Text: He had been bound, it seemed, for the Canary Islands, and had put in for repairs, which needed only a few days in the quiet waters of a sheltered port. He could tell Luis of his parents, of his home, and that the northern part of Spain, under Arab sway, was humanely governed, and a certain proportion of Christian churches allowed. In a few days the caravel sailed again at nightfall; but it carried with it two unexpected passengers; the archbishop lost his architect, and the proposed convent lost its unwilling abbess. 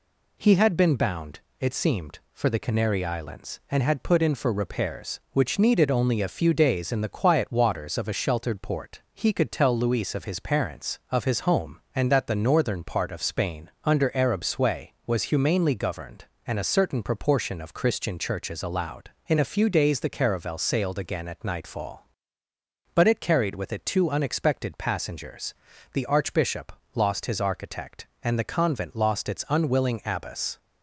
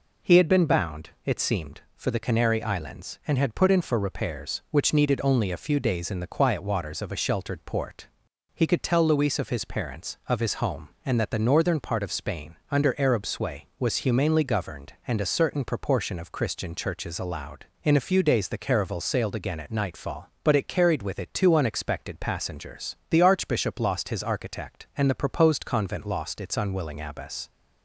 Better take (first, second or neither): second